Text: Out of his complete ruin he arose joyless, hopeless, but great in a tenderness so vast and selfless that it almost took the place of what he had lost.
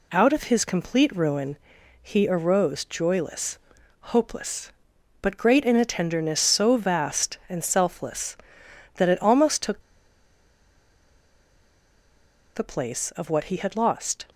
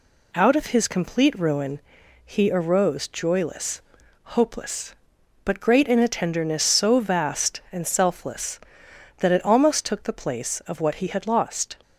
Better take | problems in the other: second | pauses between "ruin" and "he"; at 1.5 s; 0.42 s long; also in the second // pauses between "took" and "the"; strong; at 9.8 s; 2.7 s long

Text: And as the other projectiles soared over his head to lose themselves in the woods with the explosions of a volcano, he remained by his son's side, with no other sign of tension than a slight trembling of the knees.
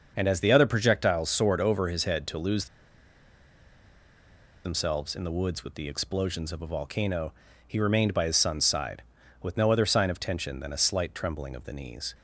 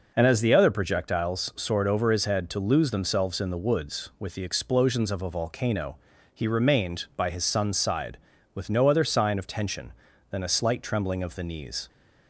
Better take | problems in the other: second | starts louder than the rest; until 1.1 s; 6.5 dB // pauses between "lose" and "themselves"; strong; at 2.6 s; 1.9 s long

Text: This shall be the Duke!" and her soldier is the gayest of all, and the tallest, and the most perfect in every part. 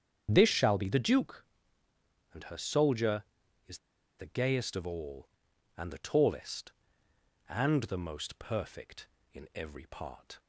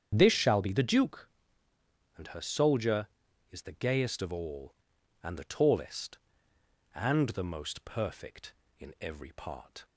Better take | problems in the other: second | starts louder than the rest; strong; until 1.3 s; 8 dB; strong in the second // pauses between "is" and "the"; at 3.7 s; 0.40 s long

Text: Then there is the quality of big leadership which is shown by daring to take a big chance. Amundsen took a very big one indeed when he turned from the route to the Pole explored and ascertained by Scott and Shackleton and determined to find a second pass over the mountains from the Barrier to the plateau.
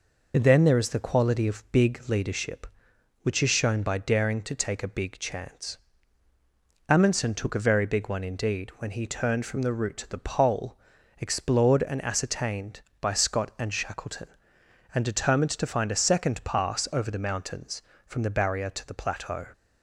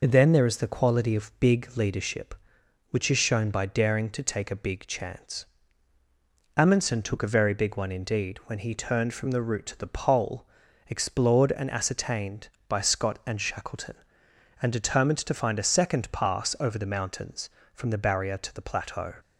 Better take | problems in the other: neither | pauses between "Pole" and "explored"; the same in both

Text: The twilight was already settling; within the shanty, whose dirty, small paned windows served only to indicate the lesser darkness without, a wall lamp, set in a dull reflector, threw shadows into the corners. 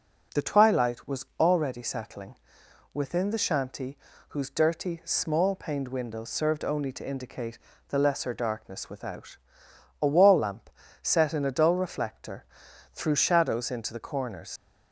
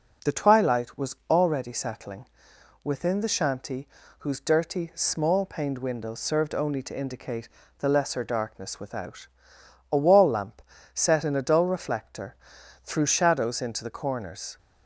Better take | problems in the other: second | pauses between "was" and "already"; slight; at 1.2 s; 0.16 s long; slight in the second // pauses between "indicate" and "the"; slight; at 7.5 s; 0.32 s long; slight in the second // leaves "corners" unfinished; at 14.5 s; 110 ms

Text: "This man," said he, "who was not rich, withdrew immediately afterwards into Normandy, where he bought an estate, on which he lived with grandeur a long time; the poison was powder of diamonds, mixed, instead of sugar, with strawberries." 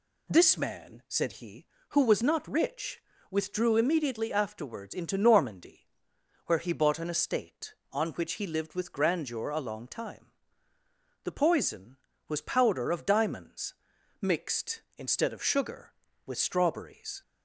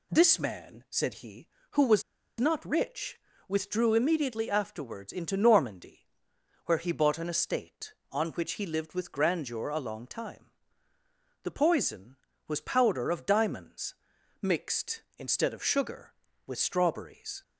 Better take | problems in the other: first | pauses between "was" and "not"; at 2.0 s; 0.37 s long

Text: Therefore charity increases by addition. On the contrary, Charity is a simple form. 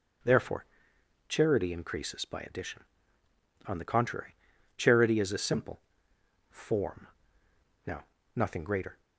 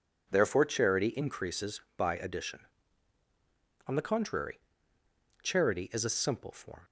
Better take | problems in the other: second | starts louder than the rest; until 1.8 s; 6.5 dB // pauses between "Therefore" and "charity"; noticeable; at 0.6 s; 0.64 s long // pauses between "simple" and "form"; noticeable; at 5.7 s; 0.72 s long // goes on to say "Now nothing greater"; noticeable; from 7.8 s on; 1.1 s long

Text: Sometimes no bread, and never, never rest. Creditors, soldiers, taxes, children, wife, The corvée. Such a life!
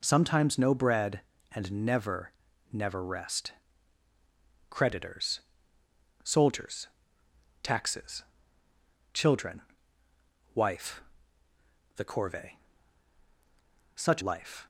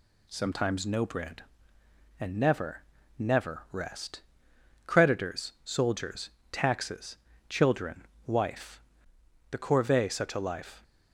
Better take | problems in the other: second | skips "a"; at 14.2 s

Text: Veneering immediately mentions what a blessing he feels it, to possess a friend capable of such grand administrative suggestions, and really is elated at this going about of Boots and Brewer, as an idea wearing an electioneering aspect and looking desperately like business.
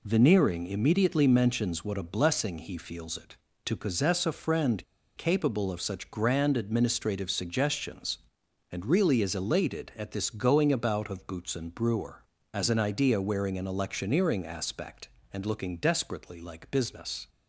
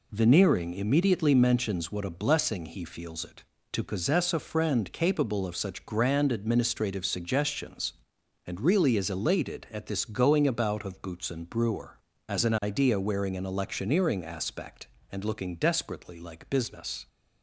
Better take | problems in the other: second | pauses between "friend" and "capable"; slight; at 4.8 s; 0.32 s long

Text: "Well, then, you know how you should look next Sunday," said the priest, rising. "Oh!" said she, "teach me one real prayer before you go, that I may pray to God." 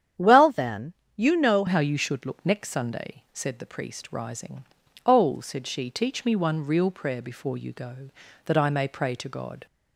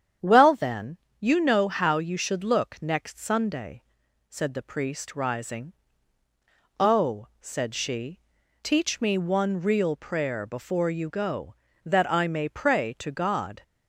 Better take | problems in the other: second | starts louder than the rest; strong; until 1.3 s; 9 dB; strong in the second // changes voice at "how"; from 1.6 s on; 8.0 s long

